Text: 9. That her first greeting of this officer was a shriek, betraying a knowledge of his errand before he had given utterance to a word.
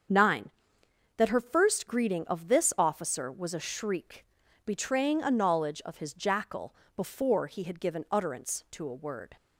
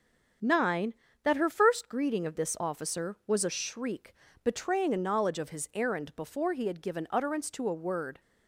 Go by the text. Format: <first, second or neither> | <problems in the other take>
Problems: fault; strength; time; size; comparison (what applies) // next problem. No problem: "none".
second | starts louder than the rest; strong; until 1.8 s; 7.5 dB; strong in the second // says "jackal" for "errand"; at 6.1 s